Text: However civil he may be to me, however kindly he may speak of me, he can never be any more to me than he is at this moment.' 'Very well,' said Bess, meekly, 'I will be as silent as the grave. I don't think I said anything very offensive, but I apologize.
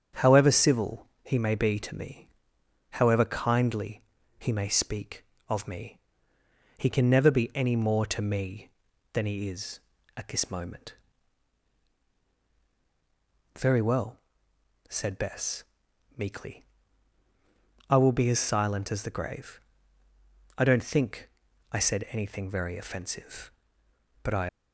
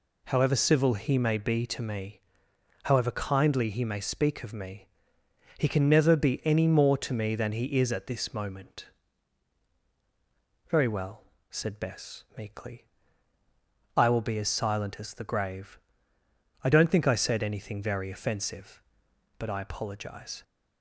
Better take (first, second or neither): second